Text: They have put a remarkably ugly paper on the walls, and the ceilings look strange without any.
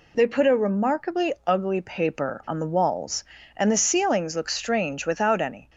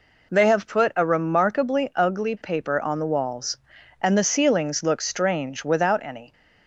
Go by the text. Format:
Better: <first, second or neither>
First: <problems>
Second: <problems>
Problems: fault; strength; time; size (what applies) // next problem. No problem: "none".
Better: second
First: skips "have"; at 0.2 s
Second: none